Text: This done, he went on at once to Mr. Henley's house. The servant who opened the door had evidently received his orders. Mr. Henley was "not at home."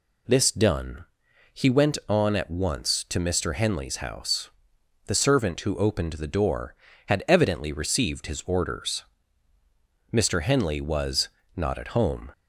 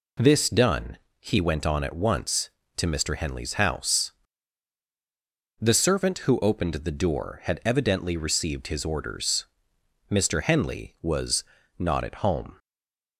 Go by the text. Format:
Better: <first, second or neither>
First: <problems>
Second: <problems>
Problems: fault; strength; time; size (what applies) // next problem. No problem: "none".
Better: first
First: pauses between "was" and "not"; slight; at 11.2 s; 0.26 s long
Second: pauses between "was" and "not"; slight; at 11.4 s; 0.34 s long // stays silent after the last word; slight; from 12.5 s on; 0.6 s long